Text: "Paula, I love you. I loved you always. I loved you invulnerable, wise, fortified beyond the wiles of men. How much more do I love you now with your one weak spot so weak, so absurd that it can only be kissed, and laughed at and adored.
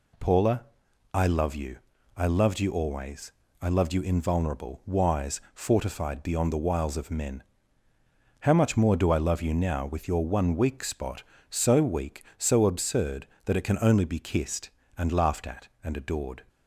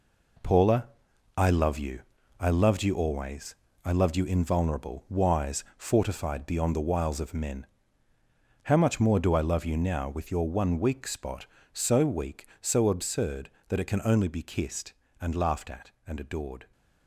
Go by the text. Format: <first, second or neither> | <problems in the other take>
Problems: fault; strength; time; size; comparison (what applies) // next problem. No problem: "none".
first | gets quieter; strong; throughout; 7.5 dB